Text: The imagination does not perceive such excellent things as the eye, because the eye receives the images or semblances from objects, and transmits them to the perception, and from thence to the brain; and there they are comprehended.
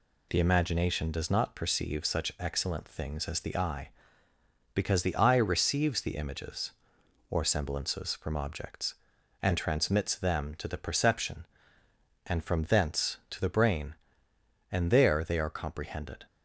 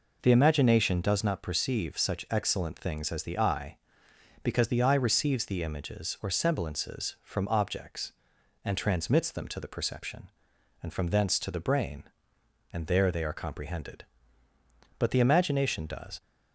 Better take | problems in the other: first | goes on to say "But the imagination does"; noticeable; from 14.9 s on; 1.2 s long

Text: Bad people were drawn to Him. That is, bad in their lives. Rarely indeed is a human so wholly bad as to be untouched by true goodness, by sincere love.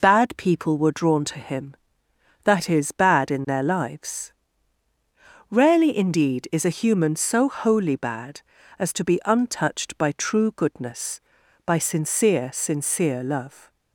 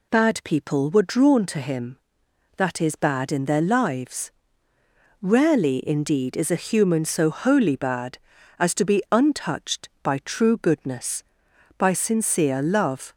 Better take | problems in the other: second | says "sincere" twice; at 12.5 s

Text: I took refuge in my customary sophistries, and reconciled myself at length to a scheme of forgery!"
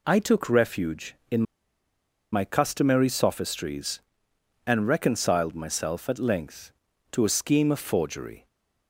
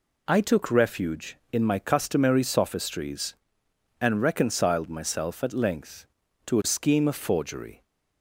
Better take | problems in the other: second | pauses between "in" and "my"; noticeable; at 1.4 s; 0.90 s long

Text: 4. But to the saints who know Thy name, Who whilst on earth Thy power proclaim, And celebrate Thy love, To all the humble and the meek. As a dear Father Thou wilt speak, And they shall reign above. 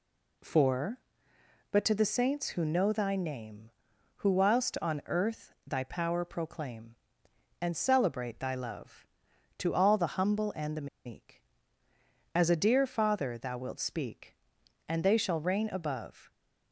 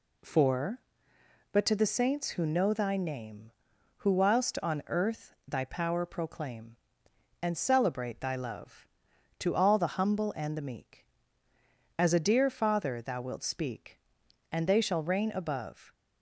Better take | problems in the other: second | pauses between "the" and "meek"; slight; at 10.8 s; 0.19 s long

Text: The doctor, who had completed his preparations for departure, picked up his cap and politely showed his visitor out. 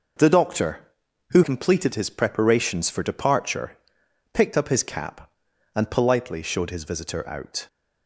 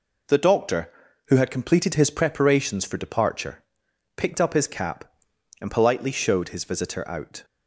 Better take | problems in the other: second | skips "had"; at 1.4 s

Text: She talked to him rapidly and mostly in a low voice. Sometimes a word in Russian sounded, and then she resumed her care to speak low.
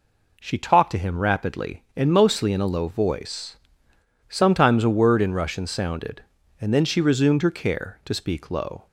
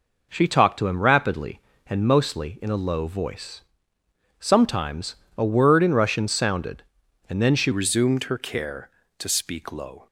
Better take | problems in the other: first | pauses between "Sometimes" and "a"; slight; at 5.1 s; 0.20 s long // changes voice at "resumed"; from 7.7 s on; 2.3 s long

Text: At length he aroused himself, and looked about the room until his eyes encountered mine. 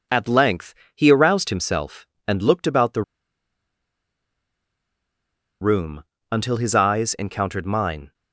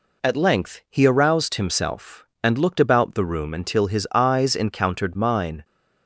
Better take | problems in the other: second | pauses between "length" and "he"; slight; at 0.7 s; 0.22 s long // pauses between "the" and "room"; strong; at 3.0 s; 2.5 s long // pauses between "room" and "until"; slight; at 6.0 s; 0.28 s long

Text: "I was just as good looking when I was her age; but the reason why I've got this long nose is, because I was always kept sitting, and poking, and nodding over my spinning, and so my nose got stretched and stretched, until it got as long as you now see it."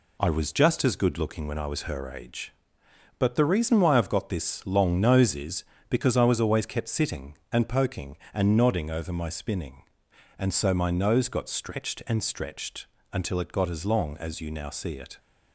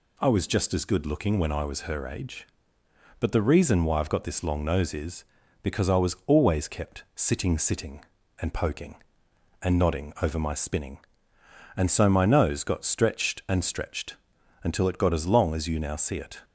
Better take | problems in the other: first | says "sitting" twice; at 7.5 s

